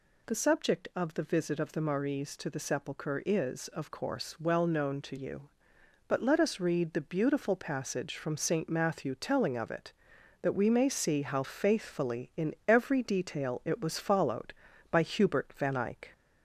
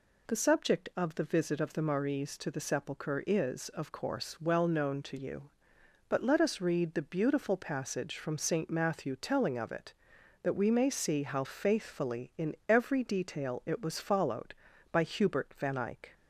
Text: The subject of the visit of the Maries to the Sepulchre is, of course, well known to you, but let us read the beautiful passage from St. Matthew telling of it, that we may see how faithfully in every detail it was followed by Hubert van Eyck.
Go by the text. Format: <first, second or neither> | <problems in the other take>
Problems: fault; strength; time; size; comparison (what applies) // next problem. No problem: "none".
second | gets louder; slight; throughout; 2 dB